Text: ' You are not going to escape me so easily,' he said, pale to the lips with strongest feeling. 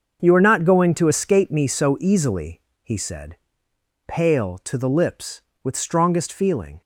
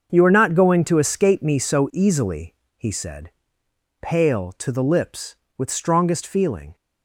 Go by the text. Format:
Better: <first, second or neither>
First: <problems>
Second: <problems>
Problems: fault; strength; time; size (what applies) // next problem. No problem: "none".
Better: neither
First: starts louder than the rest; until 1.2 s; 6.5 dB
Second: starts louder than the rest; until 1.1 s; 6.5 dB